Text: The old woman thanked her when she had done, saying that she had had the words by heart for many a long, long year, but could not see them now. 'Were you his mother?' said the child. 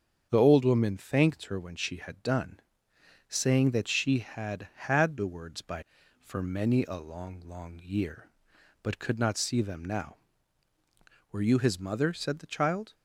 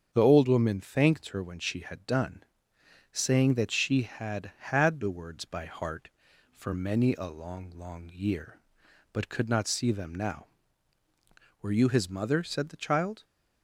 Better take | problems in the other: second | starts louder than the rest; strong; until 1.3 s; 7.5 dB; strong in the second // skips "heart"; at 6.0 s

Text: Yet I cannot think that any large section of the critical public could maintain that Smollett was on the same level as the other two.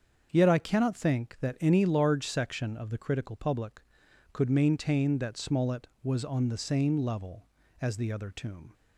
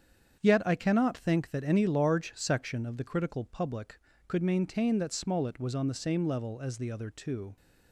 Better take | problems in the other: second | starts louder than the rest; until 1.3 s; 7 dB; strong in the second // says "tomb" for "two"; at 8.3 s

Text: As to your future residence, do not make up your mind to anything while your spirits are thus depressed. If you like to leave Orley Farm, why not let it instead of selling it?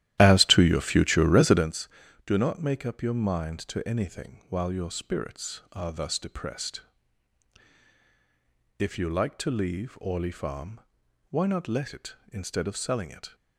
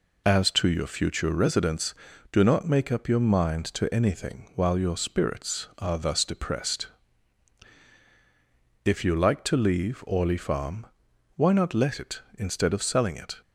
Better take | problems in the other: second | starts louder than the rest; strong; until 1.7 s; 13.5 dB

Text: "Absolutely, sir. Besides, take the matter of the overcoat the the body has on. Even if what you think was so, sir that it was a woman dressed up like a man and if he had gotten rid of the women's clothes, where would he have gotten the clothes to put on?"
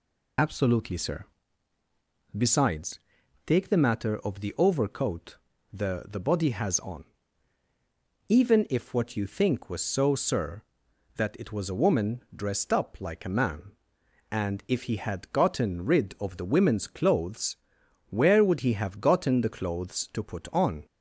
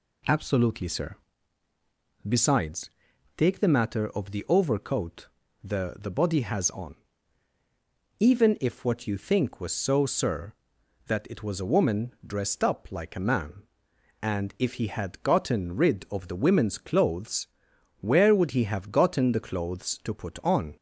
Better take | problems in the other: second | loses the start of "Absolutely"; at 0.3 s; 50 ms // pauses between "overcoat" and "the"; slight; at 5.3 s; 0.34 s long; slight in the second

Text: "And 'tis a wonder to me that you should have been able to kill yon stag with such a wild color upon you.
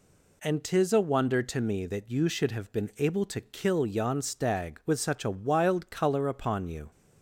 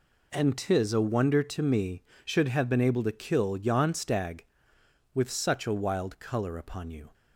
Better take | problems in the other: first | skips "that you"; at 2.1 s

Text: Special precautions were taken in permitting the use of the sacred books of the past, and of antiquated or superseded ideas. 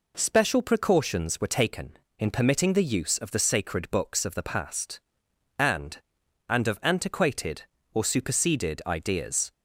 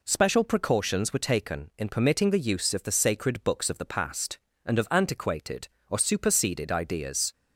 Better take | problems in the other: second | says "and" twice; at 6.4 s

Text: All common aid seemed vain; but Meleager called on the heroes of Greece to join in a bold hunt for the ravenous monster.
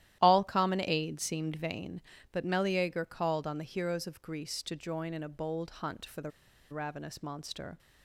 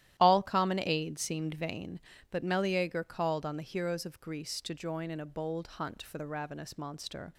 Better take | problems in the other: second | starts louder than the rest; strong; until 1.2 s; 13 dB; strong in the second // pauses between "the" and "ravenous"; at 6.3 s; 0.40 s long

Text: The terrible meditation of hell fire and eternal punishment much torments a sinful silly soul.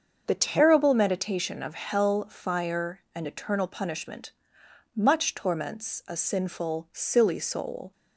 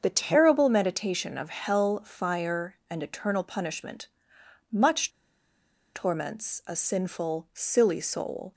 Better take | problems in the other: first | starts louder than the rest; until 1.0 s; 6.5 dB; also in the first // pauses between "punishment" and "much"; noticeable; at 4.0 s; 0.64 s long; noticeable in the first // pauses between "much" and "torments"; noticeable; at 5.1 s; 0.84 s long

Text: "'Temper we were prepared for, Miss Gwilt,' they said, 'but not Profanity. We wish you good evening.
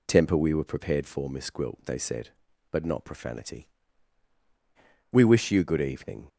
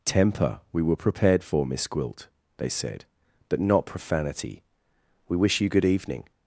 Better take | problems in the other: neither | none

